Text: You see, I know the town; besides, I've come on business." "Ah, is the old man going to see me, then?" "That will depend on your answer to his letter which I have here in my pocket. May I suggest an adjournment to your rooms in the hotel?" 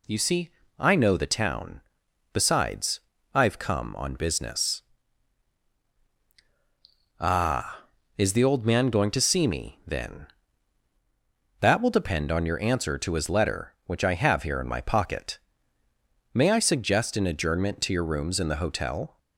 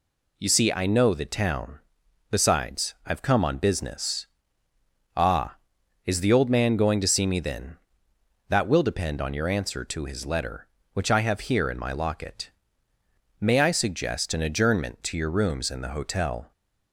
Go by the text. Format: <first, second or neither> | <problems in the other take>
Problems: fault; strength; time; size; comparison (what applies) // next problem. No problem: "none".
first | says "locket" for "pocket"; at 11.9 s